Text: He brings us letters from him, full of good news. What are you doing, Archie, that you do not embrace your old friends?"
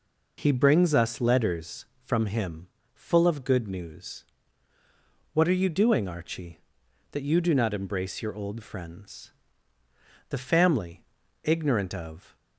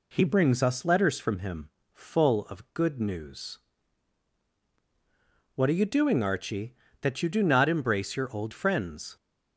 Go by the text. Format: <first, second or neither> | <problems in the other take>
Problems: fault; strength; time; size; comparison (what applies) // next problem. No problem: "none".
second | goes on to say "The family ignorant of"; strong; from 10.2 s on; 2.0 s long